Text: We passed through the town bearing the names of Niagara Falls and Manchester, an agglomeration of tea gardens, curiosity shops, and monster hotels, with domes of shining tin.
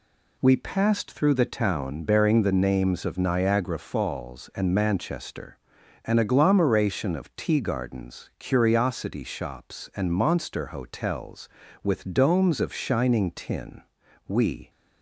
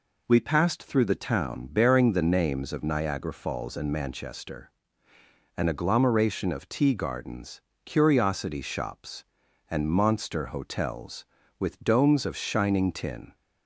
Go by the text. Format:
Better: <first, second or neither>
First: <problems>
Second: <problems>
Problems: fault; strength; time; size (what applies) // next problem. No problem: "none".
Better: second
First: goes on to say "We"; slight; from 14.2 s on; 0.42 s long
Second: none